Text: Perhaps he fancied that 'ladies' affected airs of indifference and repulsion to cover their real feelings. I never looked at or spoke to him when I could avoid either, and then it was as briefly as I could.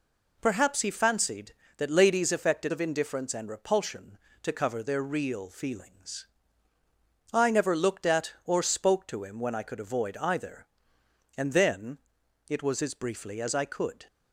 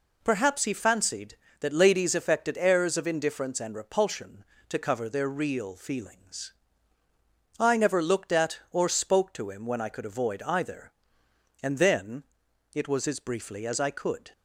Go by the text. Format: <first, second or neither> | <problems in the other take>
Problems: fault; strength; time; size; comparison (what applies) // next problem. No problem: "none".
second | skips "airs"; at 2.7 s // pauses between "then" and "it"; noticeable; at 11.9 s; 0.48 s long; noticeable in the second